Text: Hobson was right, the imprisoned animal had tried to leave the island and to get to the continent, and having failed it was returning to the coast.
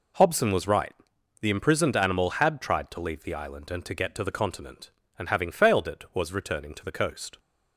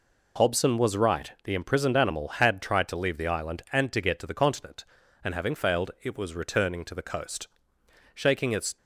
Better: first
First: none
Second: goes on to say "Shaking its"; noticeable; from 8.1 s on; 0.64 s long

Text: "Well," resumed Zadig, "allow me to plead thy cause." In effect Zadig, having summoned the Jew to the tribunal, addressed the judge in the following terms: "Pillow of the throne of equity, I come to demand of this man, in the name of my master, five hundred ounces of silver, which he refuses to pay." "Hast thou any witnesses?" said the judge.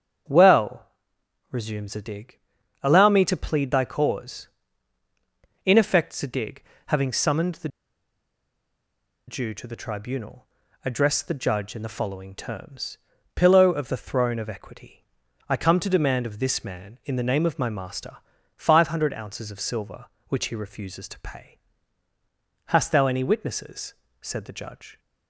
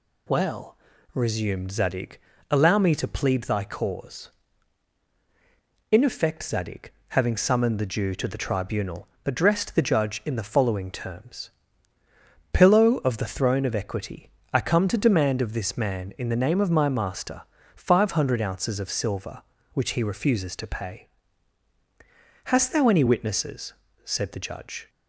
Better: second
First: starts louder than the rest; strong; until 1.9 s; 8 dB // pauses between "the" and "Jew"; strong; at 7.6 s; 1.5 s long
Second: none

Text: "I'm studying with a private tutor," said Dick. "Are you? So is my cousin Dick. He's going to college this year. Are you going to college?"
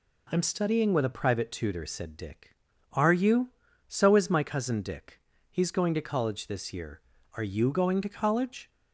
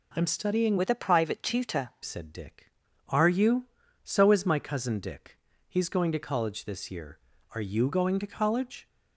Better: first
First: none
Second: changes voice from "with" to "tutor"; from 0.7 to 1.8 s; 1.1 s long

